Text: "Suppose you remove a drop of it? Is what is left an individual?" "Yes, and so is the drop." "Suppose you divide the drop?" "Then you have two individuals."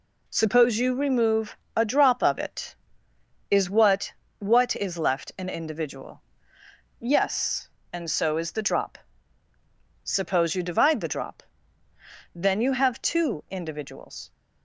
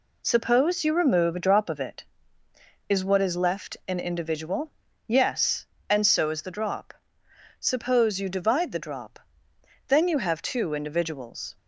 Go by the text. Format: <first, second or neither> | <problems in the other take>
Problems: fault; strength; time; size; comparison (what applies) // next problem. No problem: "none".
second | pauses between "remove" and "a"; slight; at 1.5 s; 0.20 s long // says "what" twice; at 4.4 s